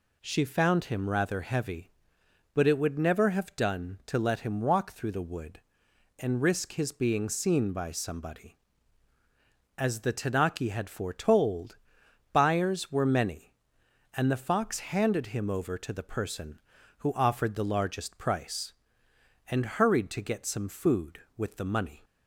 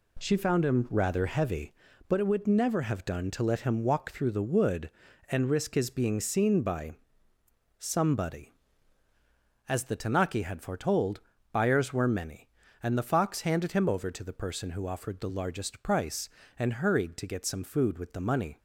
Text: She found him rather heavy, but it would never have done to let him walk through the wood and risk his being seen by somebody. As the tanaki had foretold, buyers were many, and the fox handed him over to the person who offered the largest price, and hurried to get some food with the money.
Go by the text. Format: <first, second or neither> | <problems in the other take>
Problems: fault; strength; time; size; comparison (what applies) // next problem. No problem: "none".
first | loses the start of "She"; at 0.1 s; 30 ms // pauses between "by" and "somebody"; noticeable; at 6.9 s; 0.86 s long